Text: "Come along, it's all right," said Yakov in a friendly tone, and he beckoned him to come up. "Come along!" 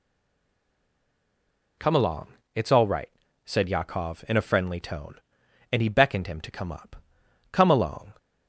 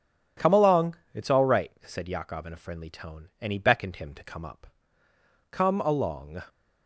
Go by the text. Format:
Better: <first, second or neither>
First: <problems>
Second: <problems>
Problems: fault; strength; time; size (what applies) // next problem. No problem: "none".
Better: second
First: stays silent before the first word; noticeable; until 1.7 s; 1.7 s long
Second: none